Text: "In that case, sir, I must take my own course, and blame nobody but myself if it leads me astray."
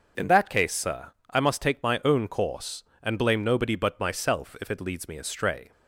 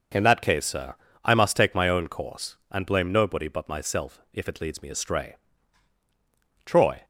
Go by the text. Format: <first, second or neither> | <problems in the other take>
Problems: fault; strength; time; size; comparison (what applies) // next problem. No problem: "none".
first | starts louder than the rest; noticeable; until 1.4 s; 6 dB // goes on to say "Troy"; slight; from 6.6 s on; 0.38 s long